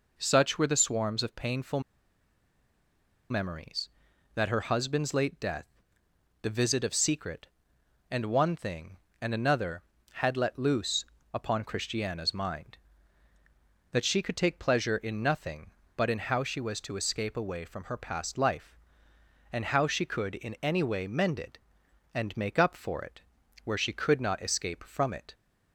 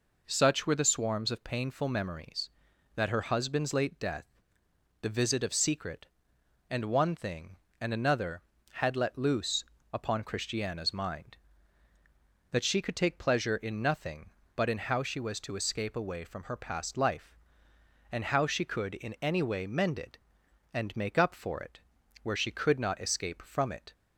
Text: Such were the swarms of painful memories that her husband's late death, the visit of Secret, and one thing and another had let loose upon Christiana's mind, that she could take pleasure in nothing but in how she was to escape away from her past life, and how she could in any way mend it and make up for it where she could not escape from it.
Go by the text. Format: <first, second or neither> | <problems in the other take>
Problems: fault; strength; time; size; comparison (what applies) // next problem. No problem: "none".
second | pauses between "painful" and "memories"; strong; at 1.8 s; 1.4 s long // pauses between "loose" and "upon"; slight; at 11.0 s; 0.26 s long; slight in the second // pauses between "it" and "where"; at 23.2 s; 0.42 s long; also in the second